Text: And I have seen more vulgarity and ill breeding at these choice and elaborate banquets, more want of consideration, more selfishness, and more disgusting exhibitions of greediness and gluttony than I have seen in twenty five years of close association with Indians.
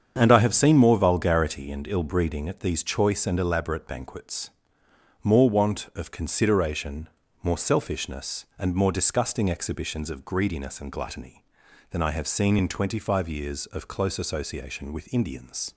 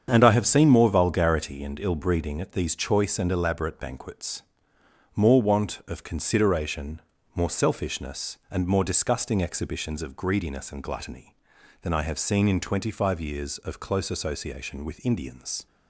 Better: neither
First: starts louder than the rest; strong; until 1.1 s; 7.5 dB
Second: starts louder than the rest; strong; until 1.1 s; 7.5 dB

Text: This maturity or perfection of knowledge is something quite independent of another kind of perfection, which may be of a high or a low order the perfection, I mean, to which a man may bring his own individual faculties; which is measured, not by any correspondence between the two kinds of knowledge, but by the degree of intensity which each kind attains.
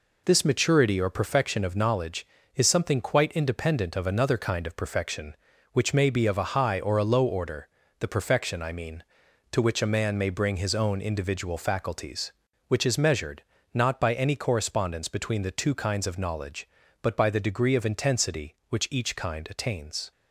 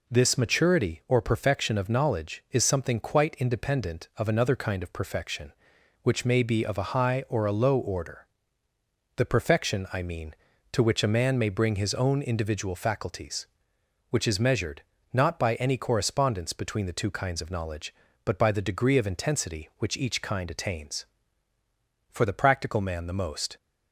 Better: first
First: pauses between "order" and "the"; slight; at 7.6 s; 0.32 s long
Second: pauses between "order" and "the"; noticeable; at 8.2 s; 0.94 s long // goes on to say "For the practical man the most"; from 22.1 s on; 1.4 s long

